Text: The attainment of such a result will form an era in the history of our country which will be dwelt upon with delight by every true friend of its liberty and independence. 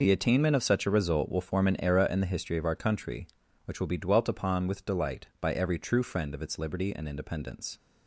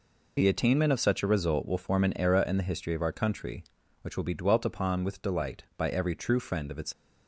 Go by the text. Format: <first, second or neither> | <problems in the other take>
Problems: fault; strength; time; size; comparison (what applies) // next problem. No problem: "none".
first | stops before "liberty and independence"; at 6.9 s